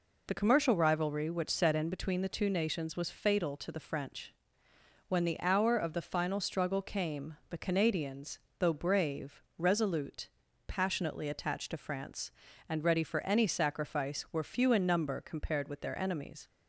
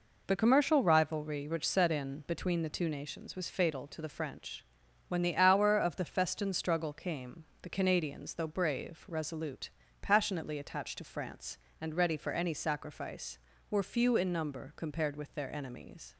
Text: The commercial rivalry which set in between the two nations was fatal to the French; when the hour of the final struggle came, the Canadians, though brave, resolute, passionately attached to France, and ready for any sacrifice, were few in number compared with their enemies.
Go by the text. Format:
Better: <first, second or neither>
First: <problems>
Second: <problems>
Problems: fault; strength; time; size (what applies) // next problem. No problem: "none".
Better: first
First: none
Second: says "festin" for "final"; at 6.0 s